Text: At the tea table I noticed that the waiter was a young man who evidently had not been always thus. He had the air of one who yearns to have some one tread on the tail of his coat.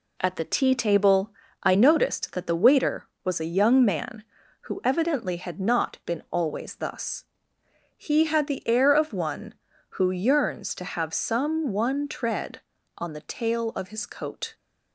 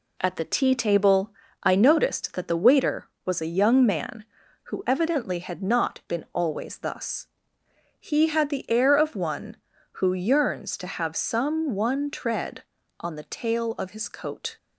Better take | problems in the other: neither | pauses between "table" and "I"; slight; the same in both

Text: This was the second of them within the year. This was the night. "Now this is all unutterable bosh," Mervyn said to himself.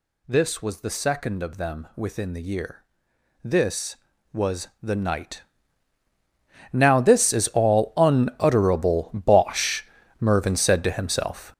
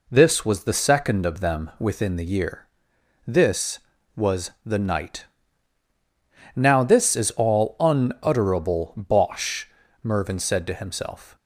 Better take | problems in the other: second | gets louder; strong; throughout; 8.5 dB

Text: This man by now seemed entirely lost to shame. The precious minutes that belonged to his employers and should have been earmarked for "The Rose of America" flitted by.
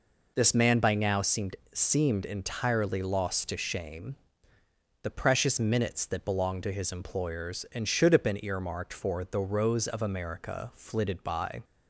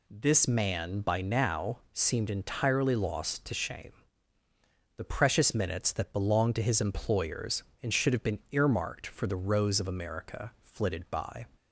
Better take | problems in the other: second | says "seemed" twice; at 1.7 s

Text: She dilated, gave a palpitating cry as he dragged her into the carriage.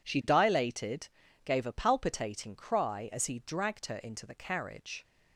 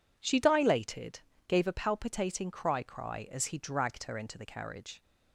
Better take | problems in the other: first | says "cry" twice; at 2.8 s

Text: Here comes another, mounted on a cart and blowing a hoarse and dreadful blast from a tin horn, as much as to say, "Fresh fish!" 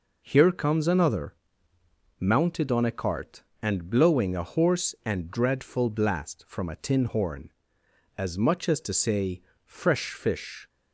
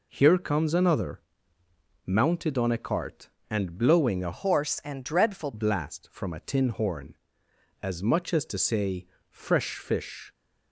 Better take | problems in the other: first | changes voice from "hoarse" to "dreadful"; from 4.3 to 5.5 s; 1.2 s long

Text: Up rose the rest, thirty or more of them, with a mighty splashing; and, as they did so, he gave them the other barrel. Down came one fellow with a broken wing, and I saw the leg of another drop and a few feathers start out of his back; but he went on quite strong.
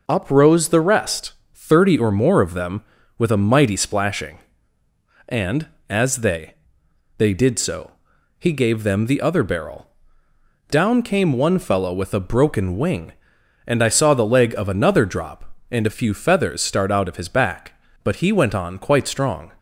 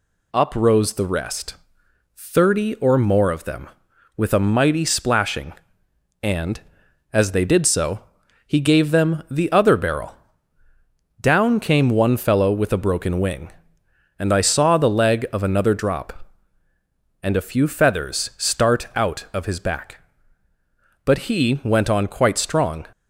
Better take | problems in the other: second | says "they" twice; at 7.1 s

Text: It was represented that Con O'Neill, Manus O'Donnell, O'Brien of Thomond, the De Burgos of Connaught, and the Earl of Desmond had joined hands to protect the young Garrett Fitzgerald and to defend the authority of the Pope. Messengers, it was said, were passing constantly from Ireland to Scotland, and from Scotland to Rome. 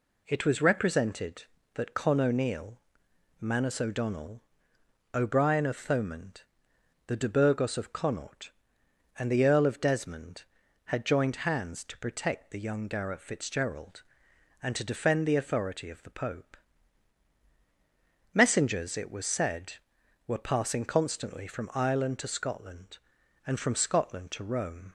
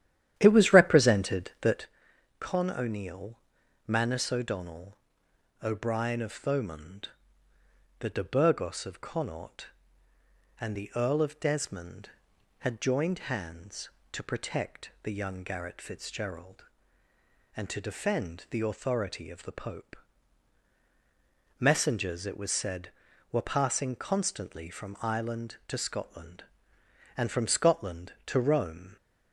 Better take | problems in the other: first | starts louder than the rest; strong; until 1.9 s; 11.5 dB // pauses between "that" and "Con"; noticeable; at 1.8 s; 0.54 s long

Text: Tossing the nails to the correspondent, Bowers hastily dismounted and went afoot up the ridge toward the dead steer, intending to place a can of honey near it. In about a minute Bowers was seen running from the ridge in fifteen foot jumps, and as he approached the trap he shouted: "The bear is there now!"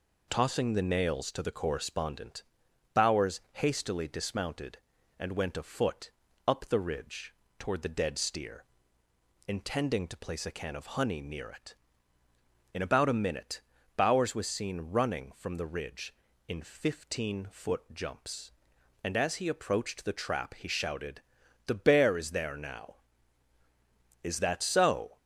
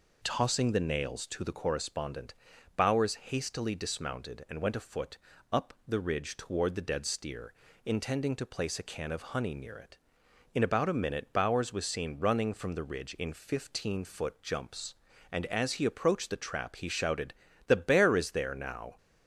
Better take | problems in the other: second | pauses between "afoot" and "up"; slight; at 6.1 s; 0.36 s long; slight in the second // pauses between "ridge" and "toward"; slight; at 7.3 s; 0.24 s long // pauses between "minute" and "Bowers"; slight; at 13.6 s; 0.36 s long // goes on to say "Is that so"; noticeable; from 24.2 s on; 0.94 s long

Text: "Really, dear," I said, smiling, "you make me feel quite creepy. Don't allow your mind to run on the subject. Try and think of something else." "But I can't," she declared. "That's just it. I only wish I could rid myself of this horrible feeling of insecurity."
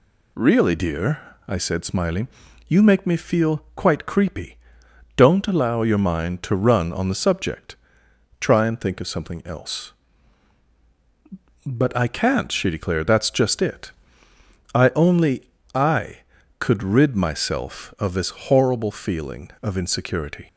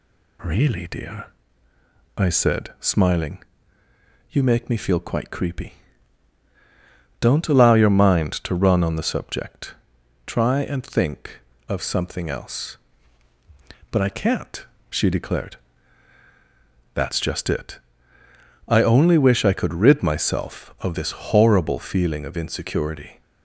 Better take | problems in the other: second | skips "wish"; at 15.6 s

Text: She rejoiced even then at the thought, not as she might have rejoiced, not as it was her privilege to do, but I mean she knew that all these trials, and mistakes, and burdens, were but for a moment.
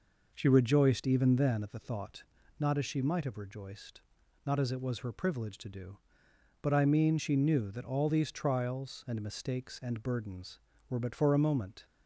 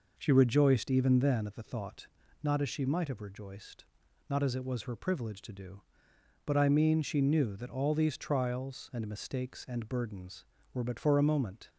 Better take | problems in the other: neither | none

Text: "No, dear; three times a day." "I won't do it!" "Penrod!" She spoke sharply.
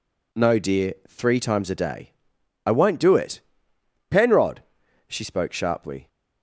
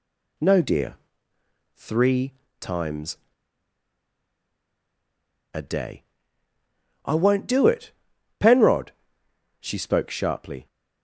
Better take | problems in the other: first | pauses between "three" and "times"; slight; at 2.3 s; 0.26 s long // pauses between "times" and "a"; strong; at 3.1 s; 2.3 s long

